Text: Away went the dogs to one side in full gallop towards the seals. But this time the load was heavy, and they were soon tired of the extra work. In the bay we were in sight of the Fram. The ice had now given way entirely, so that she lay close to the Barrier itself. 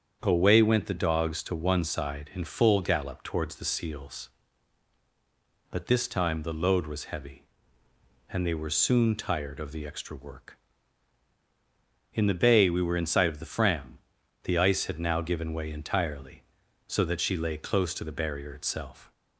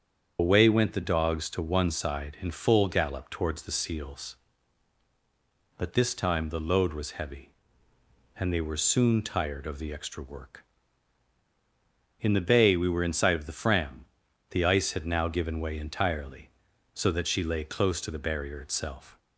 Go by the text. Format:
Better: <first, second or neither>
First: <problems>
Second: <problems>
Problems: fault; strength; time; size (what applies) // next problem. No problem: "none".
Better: first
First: starts louder than the rest; strong; until 1.2 s; 8 dB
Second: loses the start of "Away"; at 0.3 s; 110 ms // starts louder than the rest; strong; until 1.4 s; 7.5 dB